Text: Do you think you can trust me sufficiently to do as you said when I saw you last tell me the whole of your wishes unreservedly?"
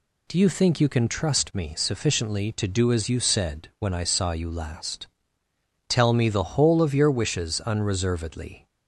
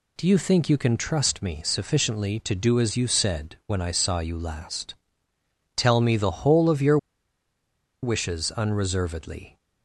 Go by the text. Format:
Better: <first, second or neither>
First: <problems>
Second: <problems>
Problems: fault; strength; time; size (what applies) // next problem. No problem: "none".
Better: first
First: pauses between "last" and "tell"; noticeable; at 5.0 s; 0.80 s long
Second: pauses between "last" and "tell"; noticeable; at 4.9 s; 0.80 s long // pauses between "your" and "wishes"; at 6.9 s; 1.0 s long